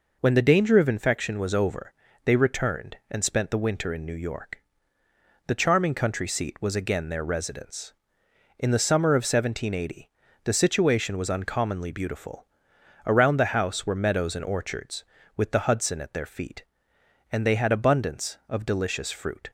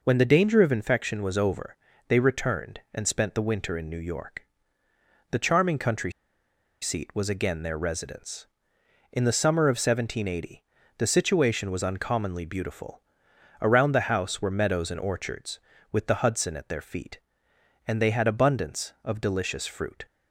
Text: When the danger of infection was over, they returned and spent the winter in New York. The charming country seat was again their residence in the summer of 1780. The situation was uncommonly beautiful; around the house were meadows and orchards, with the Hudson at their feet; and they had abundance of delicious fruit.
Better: first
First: none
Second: pauses between "country" and "seat"; noticeable; at 6.1 s; 0.69 s long

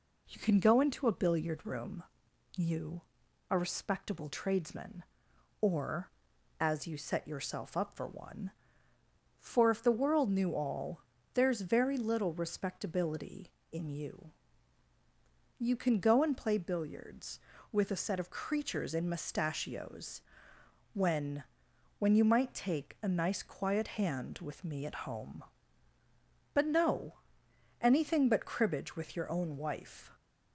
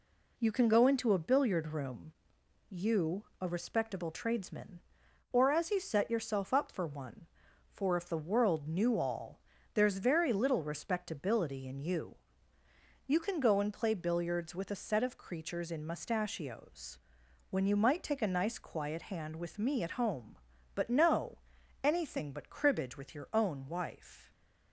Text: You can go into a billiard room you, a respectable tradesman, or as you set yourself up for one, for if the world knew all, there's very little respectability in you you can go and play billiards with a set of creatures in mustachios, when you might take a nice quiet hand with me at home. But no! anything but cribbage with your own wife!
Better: second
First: pauses between "room" and "you"; noticeable; at 2.0 s; 0.54 s long // pauses between "you" and "you"; strong; at 14.3 s; 1.2 s long // says "when" twice; at 21.9 s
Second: pauses between "room" and "you"; noticeable; at 2.1 s; 0.56 s long // pauses between "you" and "you"; noticeable; at 12.1 s; 0.90 s long

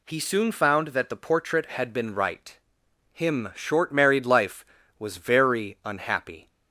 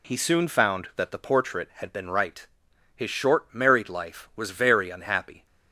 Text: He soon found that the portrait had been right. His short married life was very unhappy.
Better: second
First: says "Him" for "His"; at 3.1 s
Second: none

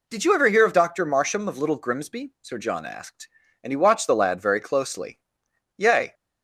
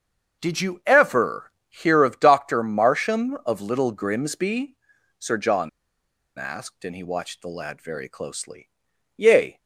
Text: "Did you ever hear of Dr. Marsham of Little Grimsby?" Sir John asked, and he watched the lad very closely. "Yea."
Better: first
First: none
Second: starts louder than the rest; until 1.4 s; 6.5 dB // pauses between "ever" and "hear"; slight; at 1.5 s; 0.18 s long // pauses between "John" and "asked"; noticeable; at 5.6 s; 0.69 s long

